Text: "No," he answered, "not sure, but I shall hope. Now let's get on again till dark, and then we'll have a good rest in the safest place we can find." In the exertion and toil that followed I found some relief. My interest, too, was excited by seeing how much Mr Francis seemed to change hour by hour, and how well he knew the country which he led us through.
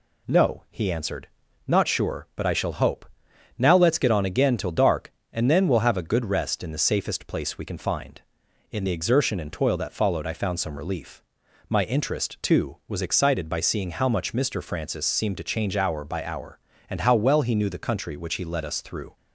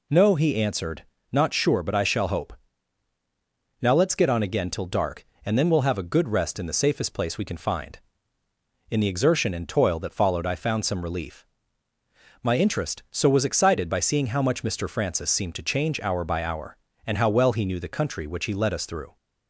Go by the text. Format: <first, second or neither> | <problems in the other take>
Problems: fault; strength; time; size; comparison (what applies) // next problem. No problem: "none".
first | says "so" for "too"; at 13.1 s